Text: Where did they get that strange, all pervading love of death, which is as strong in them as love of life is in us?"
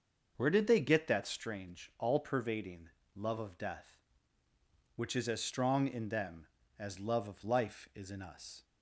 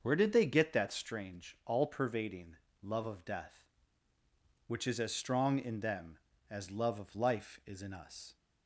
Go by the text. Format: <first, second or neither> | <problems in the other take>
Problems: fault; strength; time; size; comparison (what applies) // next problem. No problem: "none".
neither | starts louder than the rest; the same in both // pauses between "pervading" and "love"; slight; the same in both